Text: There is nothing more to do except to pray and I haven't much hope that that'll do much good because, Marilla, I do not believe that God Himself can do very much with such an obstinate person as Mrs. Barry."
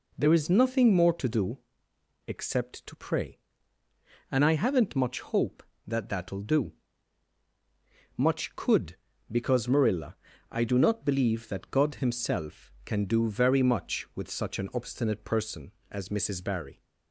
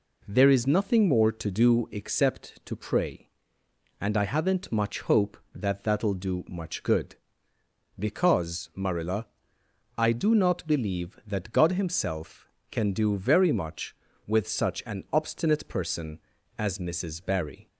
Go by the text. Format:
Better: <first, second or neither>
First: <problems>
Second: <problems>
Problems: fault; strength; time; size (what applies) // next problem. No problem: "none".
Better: second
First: pauses between "do" and "except"; noticeable; at 1.5 s; 0.70 s long // pauses between "do" and "much"; strong; at 6.7 s; 1.4 s long // says "could" for "good"; at 8.5 s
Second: none